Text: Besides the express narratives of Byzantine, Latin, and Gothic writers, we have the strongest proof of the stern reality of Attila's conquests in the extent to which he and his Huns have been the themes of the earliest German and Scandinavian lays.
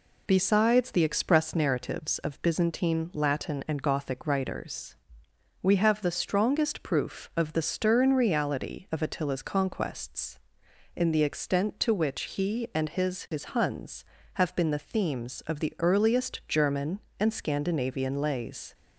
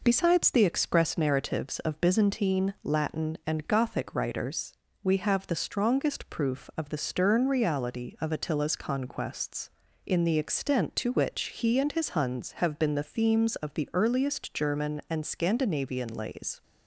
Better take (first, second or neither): second